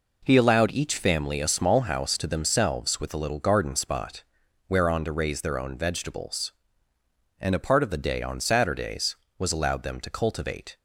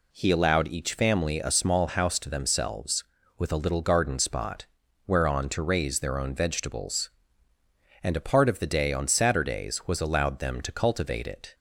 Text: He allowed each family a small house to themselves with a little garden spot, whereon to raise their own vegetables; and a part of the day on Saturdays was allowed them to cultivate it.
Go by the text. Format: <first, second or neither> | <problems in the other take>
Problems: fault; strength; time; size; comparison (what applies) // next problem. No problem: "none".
second | stops before "it"; at 10.7 s